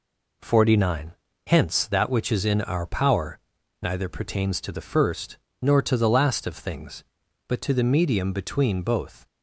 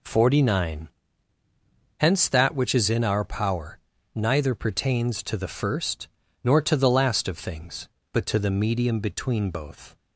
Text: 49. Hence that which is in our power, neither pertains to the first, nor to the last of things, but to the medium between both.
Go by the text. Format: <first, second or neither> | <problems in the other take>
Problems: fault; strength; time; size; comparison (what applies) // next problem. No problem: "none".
neither | none